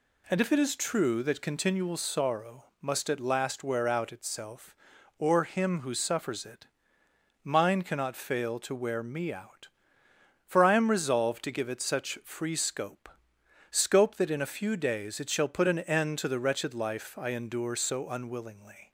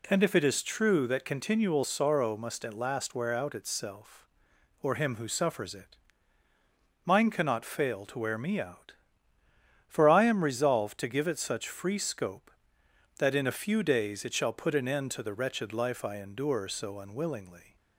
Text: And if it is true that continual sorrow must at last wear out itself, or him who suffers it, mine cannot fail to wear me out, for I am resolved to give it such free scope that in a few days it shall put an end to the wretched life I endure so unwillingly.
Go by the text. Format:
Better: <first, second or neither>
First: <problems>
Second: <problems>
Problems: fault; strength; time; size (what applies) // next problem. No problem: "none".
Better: second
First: pauses between "sorrow" and "must"; slight; at 2.6 s; 0.16 s long // says "scope" twice; at 13.6 s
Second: none